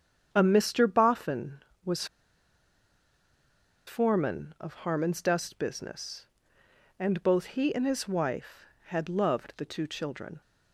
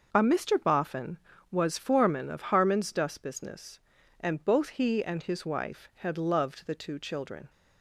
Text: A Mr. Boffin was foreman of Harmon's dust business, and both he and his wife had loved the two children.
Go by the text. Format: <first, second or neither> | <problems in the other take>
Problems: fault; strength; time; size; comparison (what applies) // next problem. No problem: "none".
second | starts louder than the rest; strong; until 1.3 s; 8.5 dB; also in the second // pauses between "was" and "foreman"; strong; at 2.0 s; 1.8 s long